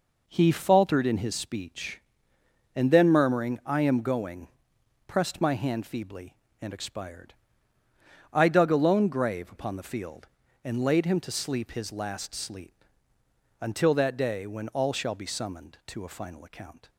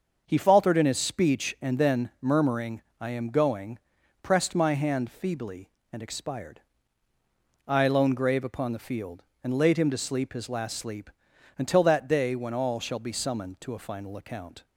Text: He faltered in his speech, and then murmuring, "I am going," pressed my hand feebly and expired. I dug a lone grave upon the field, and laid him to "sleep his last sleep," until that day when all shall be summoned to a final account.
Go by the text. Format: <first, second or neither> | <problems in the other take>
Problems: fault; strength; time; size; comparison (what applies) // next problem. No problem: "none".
first | starts louder than the rest; until 1.2 s; 6.5 dB // skips "dug a"; at 7.8 s